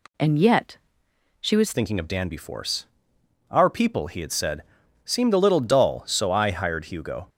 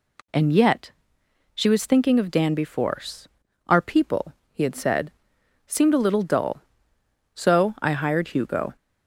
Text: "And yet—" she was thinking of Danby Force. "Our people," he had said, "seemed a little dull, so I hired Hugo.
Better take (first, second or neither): second